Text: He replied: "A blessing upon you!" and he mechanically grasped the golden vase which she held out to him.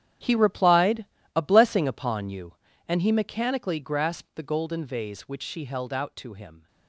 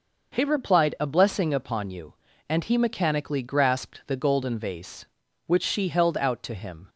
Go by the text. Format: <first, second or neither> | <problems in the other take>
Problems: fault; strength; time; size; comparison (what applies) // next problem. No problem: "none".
second | gets quieter; strong; throughout; 15.5 dB